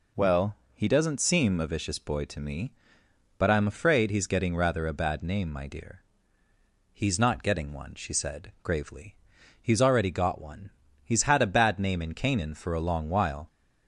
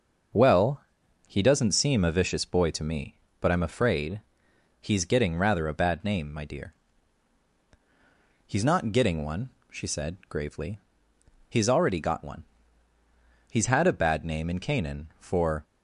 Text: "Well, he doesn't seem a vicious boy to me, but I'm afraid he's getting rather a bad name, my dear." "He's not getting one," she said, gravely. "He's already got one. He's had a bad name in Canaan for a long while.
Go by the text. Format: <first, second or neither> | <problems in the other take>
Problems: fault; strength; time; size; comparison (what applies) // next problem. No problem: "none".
first | starts louder than the rest; until 1.8 s; 6 dB // pauses between "afraid" and "he's"; noticeable; at 4.1 s; 0.62 s long // stops before "a long while"; at 15.6 s